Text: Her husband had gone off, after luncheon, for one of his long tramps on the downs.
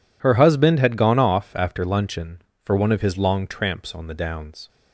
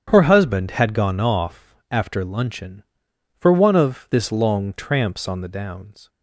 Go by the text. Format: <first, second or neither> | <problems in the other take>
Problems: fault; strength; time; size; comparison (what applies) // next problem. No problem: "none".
first | starts louder than the rest; strong; until 1.0 s; 8.5 dB // says "this" for "his"; at 4.0 s